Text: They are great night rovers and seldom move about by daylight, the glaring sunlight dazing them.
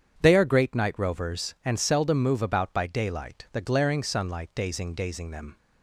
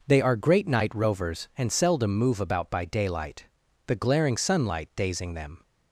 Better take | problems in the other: second | starts louder than the rest; strong; until 1.1 s; 8 dB // says "dazing" twice; at 4.9 s

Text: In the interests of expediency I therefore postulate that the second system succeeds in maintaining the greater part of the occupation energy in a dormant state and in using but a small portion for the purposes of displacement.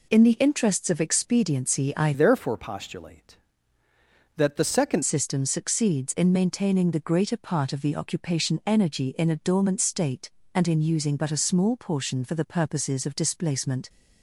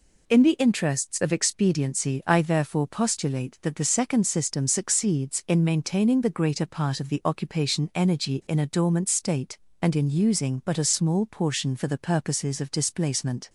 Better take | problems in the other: second | changes voice from "therefore" to "second"; from 2.1 to 5.0 s; 2.9 s long

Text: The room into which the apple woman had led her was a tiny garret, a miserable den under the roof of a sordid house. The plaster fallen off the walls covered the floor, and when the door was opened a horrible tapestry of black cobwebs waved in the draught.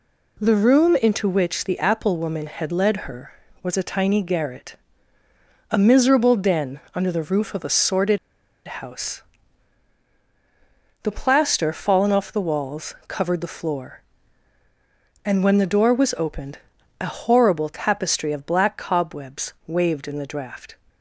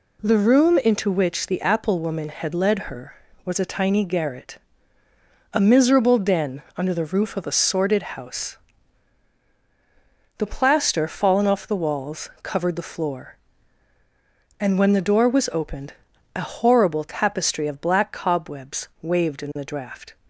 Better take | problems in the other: second | pauses between "den" and "under"; slight; at 6.7 s; 0.16 s long; slight in the second // pauses between "sordid" and "house"; noticeable; at 8.1 s; 0.49 s long // pauses between "opened" and "a"; at 16.5 s; 0.42 s long; also in the second

